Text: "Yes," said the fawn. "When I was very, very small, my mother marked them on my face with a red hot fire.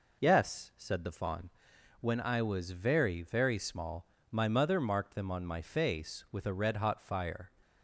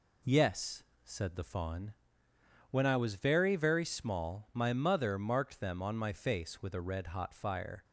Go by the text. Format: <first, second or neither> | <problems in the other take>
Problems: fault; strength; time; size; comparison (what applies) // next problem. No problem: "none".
neither | none